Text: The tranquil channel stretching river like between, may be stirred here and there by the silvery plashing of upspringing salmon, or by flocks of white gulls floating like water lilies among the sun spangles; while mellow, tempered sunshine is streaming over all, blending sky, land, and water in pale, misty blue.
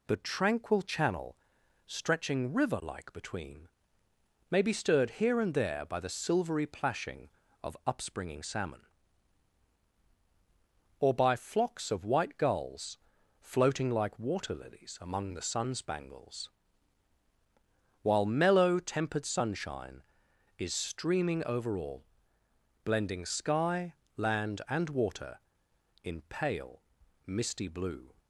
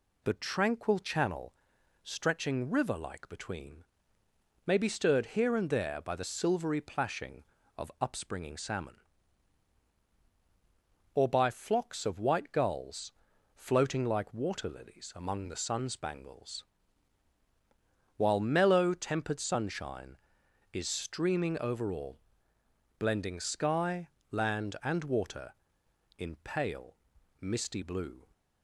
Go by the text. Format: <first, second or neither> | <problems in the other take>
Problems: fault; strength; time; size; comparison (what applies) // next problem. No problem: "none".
neither | pauses between "channel" and "stretching"; noticeable; the same in both // pauses between "gulls" and "floating"; the same in both